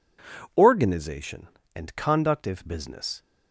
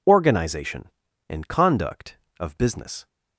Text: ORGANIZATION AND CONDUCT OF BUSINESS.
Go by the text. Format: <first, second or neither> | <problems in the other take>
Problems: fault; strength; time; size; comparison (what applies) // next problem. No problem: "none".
second | says "If" for "OF"; at 2.4 s